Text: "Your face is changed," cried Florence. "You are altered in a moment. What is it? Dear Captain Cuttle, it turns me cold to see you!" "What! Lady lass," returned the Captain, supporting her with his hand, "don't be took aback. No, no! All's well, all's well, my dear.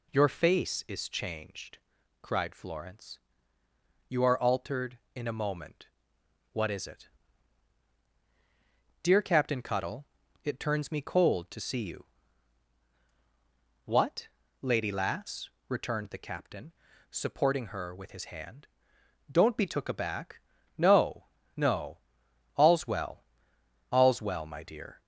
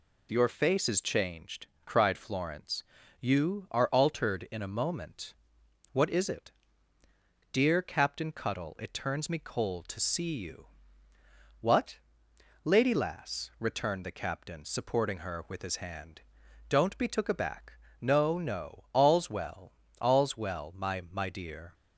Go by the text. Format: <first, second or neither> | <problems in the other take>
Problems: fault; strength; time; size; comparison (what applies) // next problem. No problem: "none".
first | says "my" twice; at 21.0 s